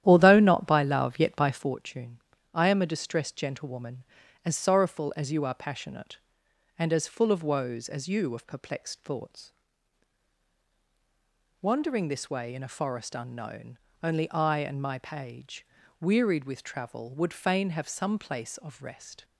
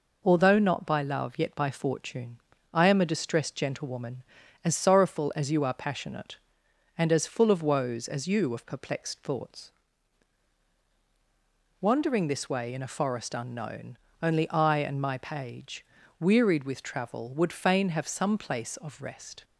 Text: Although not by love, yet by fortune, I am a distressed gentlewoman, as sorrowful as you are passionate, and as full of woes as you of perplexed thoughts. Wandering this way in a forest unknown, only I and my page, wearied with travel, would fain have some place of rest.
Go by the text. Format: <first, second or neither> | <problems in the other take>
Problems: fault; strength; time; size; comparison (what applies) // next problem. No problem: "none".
second | starts louder than the rest; strong; until 1.7 s; 11.5 dB